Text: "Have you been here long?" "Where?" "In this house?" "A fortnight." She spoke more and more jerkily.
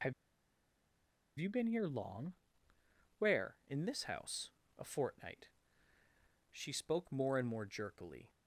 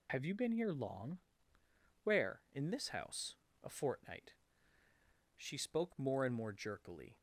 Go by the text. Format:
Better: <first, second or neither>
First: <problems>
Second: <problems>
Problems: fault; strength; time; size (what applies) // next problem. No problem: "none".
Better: second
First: pauses between "Have" and "you"; strong; at 0.1 s; 1.2 s long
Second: none